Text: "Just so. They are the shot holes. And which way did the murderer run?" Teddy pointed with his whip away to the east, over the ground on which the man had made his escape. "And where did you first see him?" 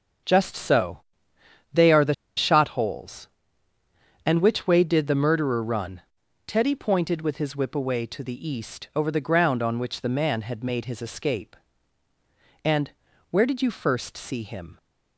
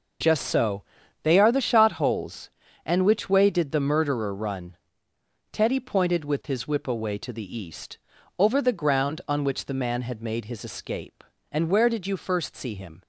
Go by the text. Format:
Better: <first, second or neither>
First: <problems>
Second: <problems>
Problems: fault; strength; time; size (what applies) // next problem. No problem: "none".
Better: second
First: starts louder than the rest; until 1.9 s; 6.5 dB // pauses between "the" and "shot"; slight; at 2.1 s; 0.23 s long // pauses between "And" and "where"; at 12.9 s; 0.40 s long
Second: none